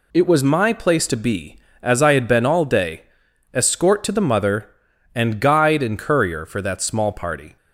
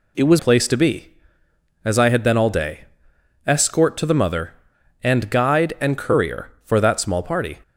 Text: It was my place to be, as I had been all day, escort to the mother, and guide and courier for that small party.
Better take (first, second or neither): first